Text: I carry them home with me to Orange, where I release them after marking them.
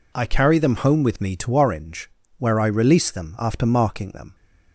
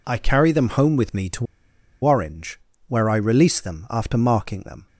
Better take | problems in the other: first | pauses between "to" and "Orange"; noticeable; at 1.4 s; 0.58 s long

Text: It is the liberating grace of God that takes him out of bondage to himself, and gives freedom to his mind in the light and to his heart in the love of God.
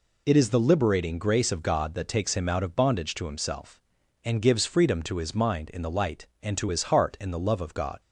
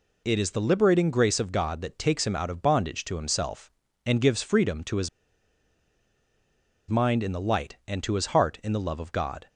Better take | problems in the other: first | pauses between "his" and "mind"; strong; at 5.0 s; 1.8 s long

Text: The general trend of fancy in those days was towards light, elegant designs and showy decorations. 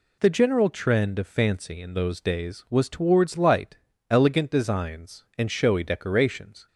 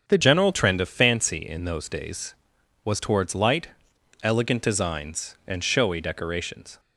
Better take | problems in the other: first | starts louder than the rest; strong; until 1.1 s; 7.5 dB // changes voice at "general"; from 0.2 s on; 6.5 s long

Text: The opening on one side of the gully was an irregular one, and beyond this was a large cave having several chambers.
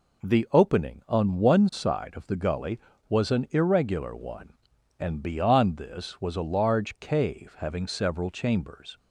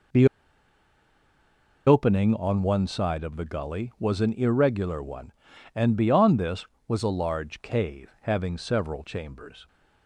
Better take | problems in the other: first | pauses between "The" and "opening"; strong; at 0.2 s; 1.6 s long

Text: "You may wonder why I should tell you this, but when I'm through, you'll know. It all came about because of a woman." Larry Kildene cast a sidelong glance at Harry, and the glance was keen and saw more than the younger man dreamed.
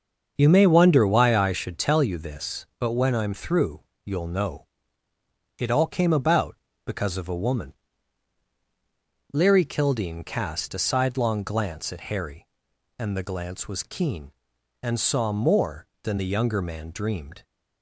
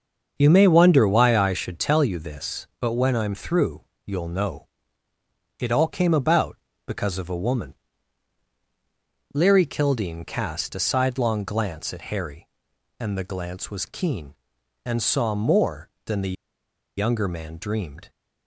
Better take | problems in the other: first | starts louder than the rest; until 1.3 s; 6.5 dB; also in the first // pauses between "the" and "younger"; noticeable; at 16.3 s; 0.64 s long

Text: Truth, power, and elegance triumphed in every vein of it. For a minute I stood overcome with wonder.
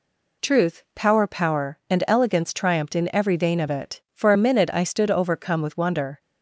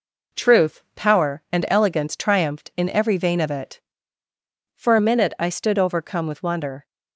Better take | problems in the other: second | says "power" twice; at 1.2 s

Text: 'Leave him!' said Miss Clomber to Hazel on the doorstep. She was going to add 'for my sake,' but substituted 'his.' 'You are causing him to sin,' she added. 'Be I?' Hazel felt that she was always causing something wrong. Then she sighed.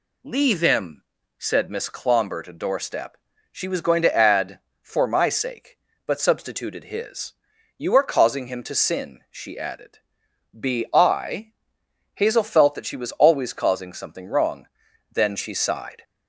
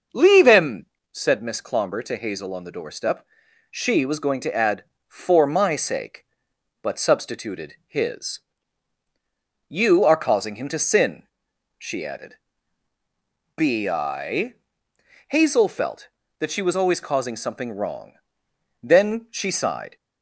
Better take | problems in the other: second | skips "Hazel on the"; at 2.5 s

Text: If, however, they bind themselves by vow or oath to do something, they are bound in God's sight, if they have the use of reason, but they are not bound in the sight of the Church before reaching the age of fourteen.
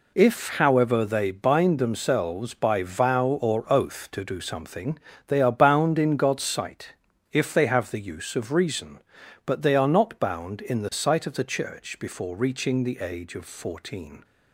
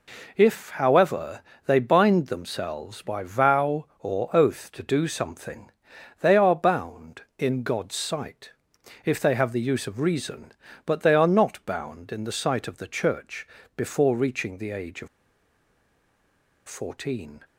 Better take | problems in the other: first | pauses between "Church" and "before"; slight; at 13.4 s; 0.30 s long // pauses between "of" and "fourteen"; strong; at 15.0 s; 1.6 s long

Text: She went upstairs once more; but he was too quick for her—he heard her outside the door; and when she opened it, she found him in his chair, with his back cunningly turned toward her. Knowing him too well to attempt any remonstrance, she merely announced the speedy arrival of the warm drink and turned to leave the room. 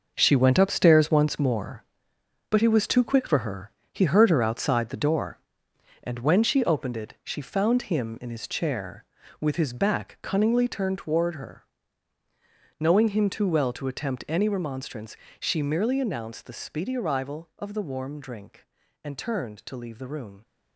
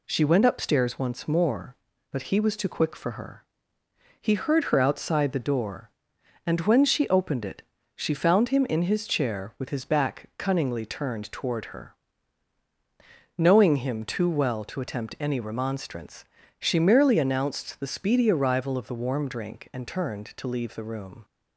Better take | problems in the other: second | gets quieter; strong; throughout; 10 dB

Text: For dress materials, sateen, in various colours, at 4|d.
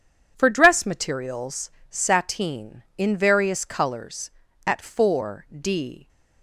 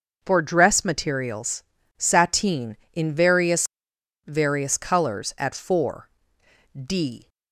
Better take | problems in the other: first | says "various" twice; at 4.2 s

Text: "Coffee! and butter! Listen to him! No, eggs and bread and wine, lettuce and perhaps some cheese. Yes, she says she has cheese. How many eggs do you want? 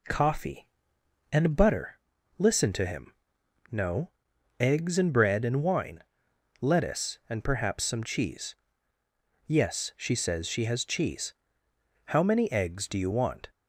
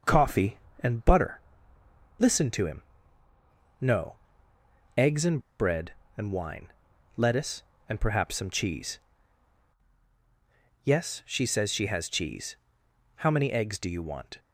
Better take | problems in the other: first | starts louder than the rest; until 1.2 s; 6 dB // pauses between "and" and "bread"; slight; at 5.3 s; 0.20 s long

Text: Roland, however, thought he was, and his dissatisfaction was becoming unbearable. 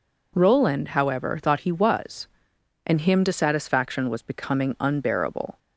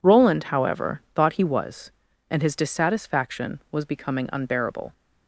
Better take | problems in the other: second | says "him" for "his"; at 3.0 s

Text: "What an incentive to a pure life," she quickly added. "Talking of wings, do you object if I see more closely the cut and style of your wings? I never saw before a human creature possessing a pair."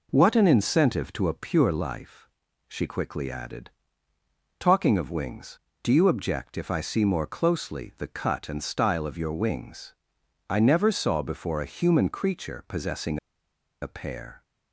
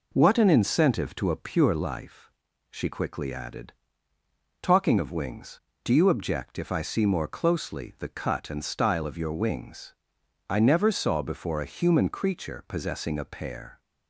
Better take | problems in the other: second | pauses between "possessing" and "a"; noticeable; at 13.1 s; 0.63 s long

